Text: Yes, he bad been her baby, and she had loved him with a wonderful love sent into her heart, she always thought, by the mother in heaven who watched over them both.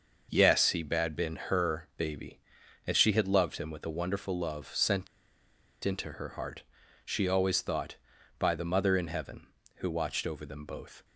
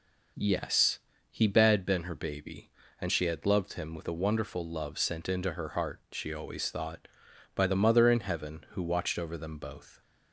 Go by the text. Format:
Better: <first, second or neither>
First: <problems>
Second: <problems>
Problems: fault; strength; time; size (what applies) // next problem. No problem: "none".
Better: second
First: starts louder than the rest; noticeable; until 1.3 s; 6 dB // pauses between "sent" and "into"; noticeable; at 5.0 s; 0.77 s long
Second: none